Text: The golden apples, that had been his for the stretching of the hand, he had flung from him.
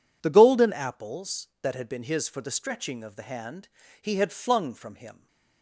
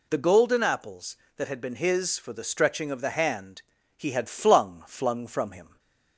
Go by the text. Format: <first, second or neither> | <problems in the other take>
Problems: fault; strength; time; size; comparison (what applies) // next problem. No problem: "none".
first | says "flung" twice; at 4.8 s // stays silent after the last word; slight; from 5.6 s on; 0.5 s long; slight in the first